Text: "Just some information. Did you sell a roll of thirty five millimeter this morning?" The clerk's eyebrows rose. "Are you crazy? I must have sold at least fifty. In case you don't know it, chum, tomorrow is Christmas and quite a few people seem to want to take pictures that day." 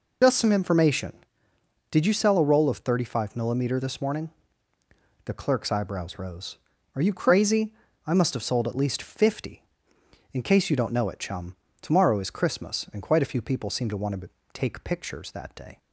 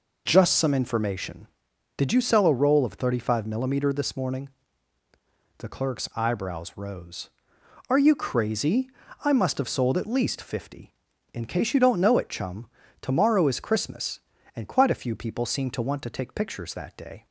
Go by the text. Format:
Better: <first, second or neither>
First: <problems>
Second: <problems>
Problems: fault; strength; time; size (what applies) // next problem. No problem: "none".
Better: second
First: loses the start of "Just"; at 0.2 s; 60 ms // pauses between "to" and "take"; slight; at 14.2 s; 0.24 s long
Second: none